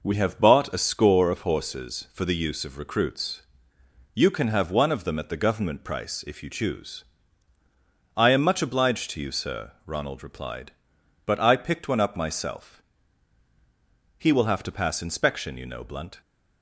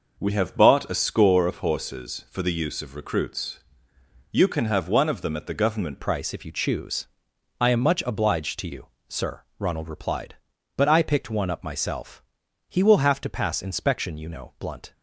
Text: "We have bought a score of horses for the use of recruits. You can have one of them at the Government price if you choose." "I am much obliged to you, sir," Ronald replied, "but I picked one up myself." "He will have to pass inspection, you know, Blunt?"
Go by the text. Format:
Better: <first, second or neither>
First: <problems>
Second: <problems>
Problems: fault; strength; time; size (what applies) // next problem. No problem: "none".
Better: first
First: none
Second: changes voice at "price"; from 6.0 s on; 8.9 s long